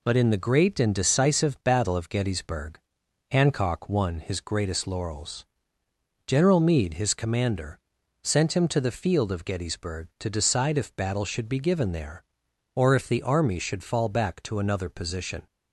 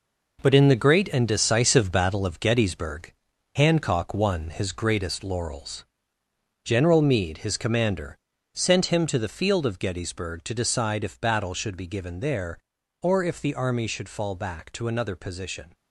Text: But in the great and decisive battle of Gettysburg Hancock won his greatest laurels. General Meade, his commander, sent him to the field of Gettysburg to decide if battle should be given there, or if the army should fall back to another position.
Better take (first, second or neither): first